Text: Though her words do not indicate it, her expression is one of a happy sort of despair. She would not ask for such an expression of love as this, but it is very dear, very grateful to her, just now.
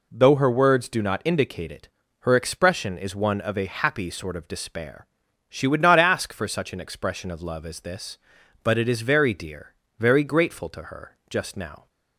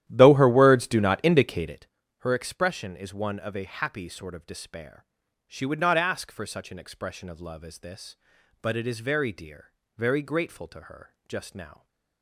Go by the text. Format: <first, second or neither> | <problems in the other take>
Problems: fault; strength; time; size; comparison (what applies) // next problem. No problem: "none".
first | starts louder than the rest; strong; until 1.9 s; 12 dB